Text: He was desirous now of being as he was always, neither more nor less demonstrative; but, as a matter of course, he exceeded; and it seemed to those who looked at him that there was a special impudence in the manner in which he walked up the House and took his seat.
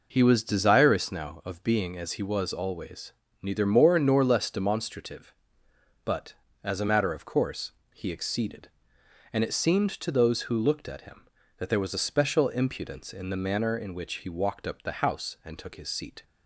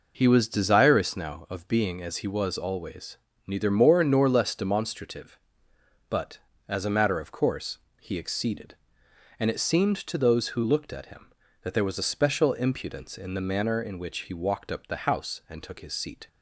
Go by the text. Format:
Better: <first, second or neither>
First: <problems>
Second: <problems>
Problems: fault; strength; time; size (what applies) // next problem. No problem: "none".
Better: neither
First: none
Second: none